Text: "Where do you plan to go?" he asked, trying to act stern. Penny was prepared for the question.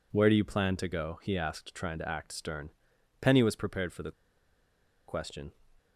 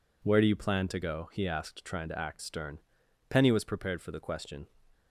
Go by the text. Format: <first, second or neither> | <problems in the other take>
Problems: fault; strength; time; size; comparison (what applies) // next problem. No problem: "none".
second | pauses between "the" and "question"; noticeable; at 4.1 s; 0.96 s long